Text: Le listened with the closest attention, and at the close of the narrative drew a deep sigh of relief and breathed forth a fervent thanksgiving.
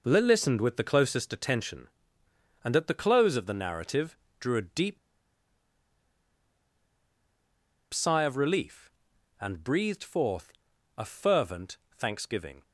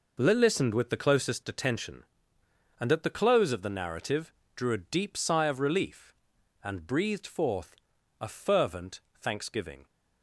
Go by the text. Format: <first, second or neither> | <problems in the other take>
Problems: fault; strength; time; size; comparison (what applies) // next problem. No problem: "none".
second | pauses between "narrative" and "drew"; slight; at 4.1 s; 0.24 s long; slight in the second // pauses between "deep" and "sigh"; strong; at 4.9 s; 2.9 s long // pauses between "forth" and "a"; at 10.5 s; 0.44 s long; also in the second // pauses between "fervent" and "thanksgiving"; slight; at 11.7 s; 0.18 s long; slight in the second